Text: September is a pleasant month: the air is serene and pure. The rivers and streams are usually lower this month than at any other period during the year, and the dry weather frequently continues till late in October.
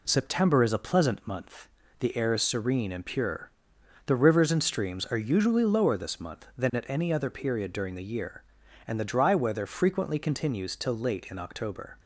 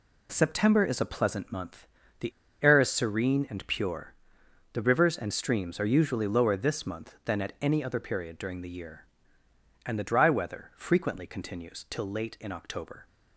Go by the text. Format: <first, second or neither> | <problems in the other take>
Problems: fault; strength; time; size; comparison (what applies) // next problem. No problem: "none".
first | pauses between "the" and "air"; slight; at 2.3 s; 0.32 s long